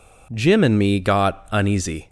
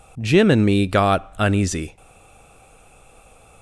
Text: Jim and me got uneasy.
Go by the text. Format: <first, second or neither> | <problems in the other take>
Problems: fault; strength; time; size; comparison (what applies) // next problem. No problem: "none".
first | stays silent after the last word; noticeable; from 1.9 s on; 1.7 s long